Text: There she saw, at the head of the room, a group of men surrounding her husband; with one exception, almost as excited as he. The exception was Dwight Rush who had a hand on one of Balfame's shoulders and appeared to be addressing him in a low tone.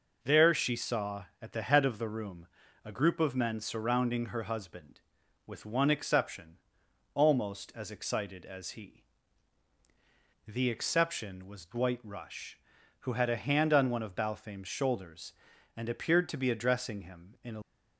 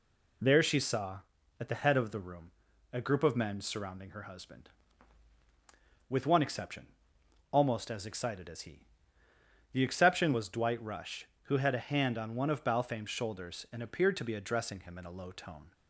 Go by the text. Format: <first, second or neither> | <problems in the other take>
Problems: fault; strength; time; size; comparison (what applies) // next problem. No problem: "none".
second | stops before "low tone"; at 17.6 s